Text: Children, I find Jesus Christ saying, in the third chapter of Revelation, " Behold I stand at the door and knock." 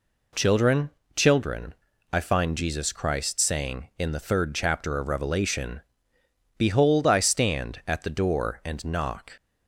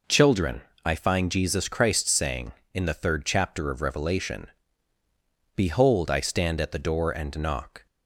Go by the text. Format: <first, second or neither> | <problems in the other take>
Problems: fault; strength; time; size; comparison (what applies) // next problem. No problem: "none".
second | says "Children" twice; at 1.1 s